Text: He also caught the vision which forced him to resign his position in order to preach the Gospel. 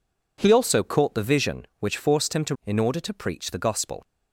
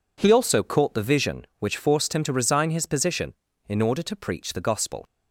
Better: second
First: skips "resign his position"; at 2.6 s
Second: none

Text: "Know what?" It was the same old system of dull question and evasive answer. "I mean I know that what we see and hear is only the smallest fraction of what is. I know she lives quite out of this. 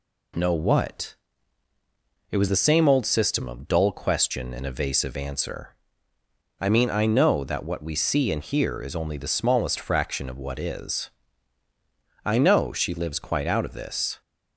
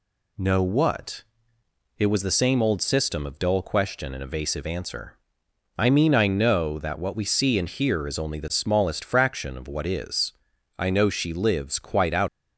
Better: first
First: none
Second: stops before "of this"; at 12.2 s

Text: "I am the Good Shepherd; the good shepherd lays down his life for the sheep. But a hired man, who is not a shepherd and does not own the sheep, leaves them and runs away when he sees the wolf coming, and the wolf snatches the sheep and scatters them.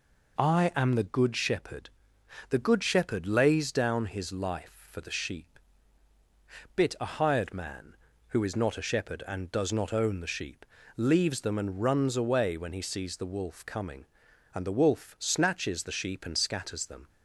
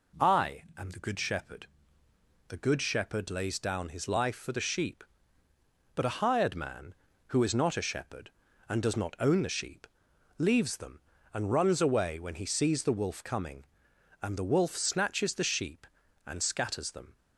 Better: second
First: says "Bit" for "But"; at 6.7 s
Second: none

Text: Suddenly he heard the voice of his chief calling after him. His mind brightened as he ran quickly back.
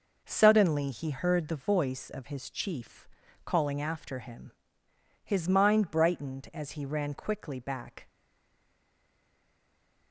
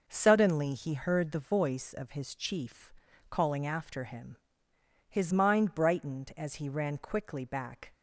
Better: second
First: pauses between "chief" and "calling"; slight; at 3.0 s; 0.36 s long // stays silent after the last word; noticeable; from 8.0 s on; 2.1 s long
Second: pauses between "chief" and "calling"; slight; at 2.9 s; 0.36 s long

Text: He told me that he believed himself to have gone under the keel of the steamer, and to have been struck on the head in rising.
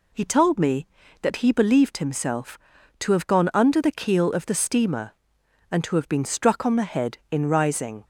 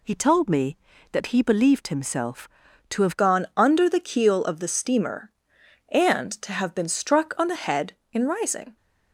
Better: first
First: none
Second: changes voice at "gone"; from 3.1 s on; 5.6 s long

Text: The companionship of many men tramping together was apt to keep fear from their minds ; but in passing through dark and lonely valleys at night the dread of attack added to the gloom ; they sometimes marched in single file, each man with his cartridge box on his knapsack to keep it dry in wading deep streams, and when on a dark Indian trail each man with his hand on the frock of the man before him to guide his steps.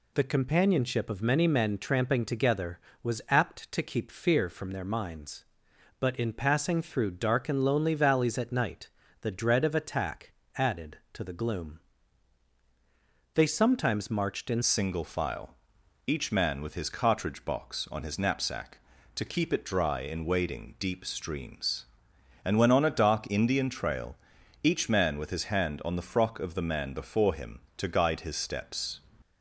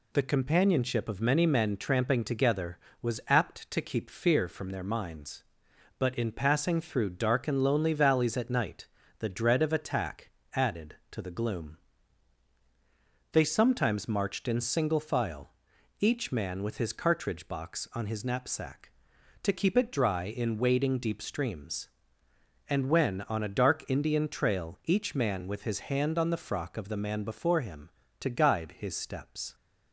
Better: second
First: pauses between "night" and "the"; slight; at 8.8 s; 0.32 s long // pauses between "attack" and "added"; slight; at 10.3 s; 0.22 s long // changes voice at "single"; from 14.6 s on; 14.3 s long // pauses between "trail" and "each"; noticeable; at 24.1 s; 0.48 s long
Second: pauses between "night" and "the"; slight; at 8.8 s; 0.32 s long // pauses between "attack" and "added"; slight; at 10.3 s; 0.22 s long

